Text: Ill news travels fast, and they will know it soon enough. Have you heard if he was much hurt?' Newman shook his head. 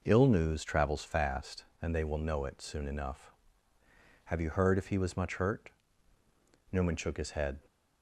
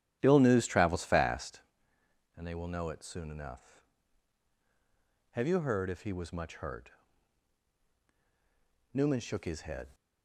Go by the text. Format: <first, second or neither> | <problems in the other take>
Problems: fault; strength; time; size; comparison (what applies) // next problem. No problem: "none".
first | starts louder than the rest; strong; until 1.8 s; 11 dB